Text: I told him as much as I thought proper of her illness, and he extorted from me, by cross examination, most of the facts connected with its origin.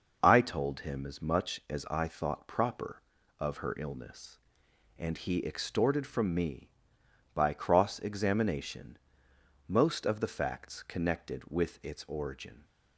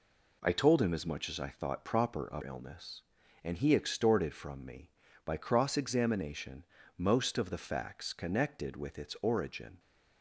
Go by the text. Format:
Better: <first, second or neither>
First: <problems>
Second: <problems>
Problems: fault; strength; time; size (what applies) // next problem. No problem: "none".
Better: first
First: none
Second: skips "her"; at 2.4 s